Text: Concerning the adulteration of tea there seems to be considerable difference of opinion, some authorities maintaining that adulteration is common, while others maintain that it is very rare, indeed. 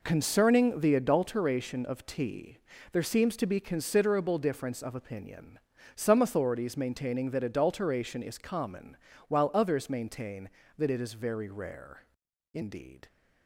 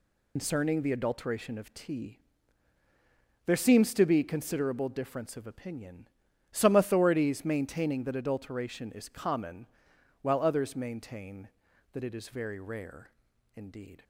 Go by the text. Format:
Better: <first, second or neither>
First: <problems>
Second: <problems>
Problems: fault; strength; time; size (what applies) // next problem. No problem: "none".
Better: first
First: pauses between "tea" and "there"; slight; at 2.5 s; 0.34 s long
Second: loses the start of "Concerning"; at 0.3 s; 95 ms // pauses between "tea" and "there"; strong; at 2.1 s; 1.2 s long